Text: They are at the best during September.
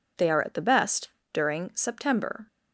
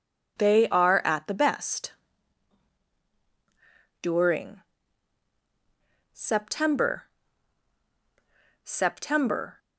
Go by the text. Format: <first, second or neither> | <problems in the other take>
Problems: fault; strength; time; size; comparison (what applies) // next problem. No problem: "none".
first | pauses between "best" and "during"; strong; at 1.9 s; 2.1 s long; slight in the first // pauses between "during" and "September"; strong; at 4.6 s; 1.5 s long // says "September" twice; at 8.6 s